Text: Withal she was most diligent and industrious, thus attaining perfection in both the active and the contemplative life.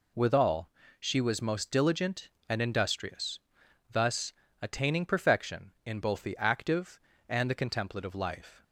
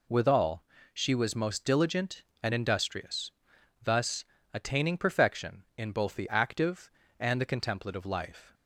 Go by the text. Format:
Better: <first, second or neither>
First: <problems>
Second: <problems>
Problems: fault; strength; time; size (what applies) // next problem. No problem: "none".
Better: neither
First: pauses between "Withal" and "she"; slight; at 0.6 s; 0.30 s long // pauses between "thus" and "attaining"; slight; at 4.3 s; 0.30 s long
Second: pauses between "Withal" and "she"; slight; at 0.6 s; 0.30 s long // pauses between "thus" and "attaining"; slight; at 4.2 s; 0.30 s long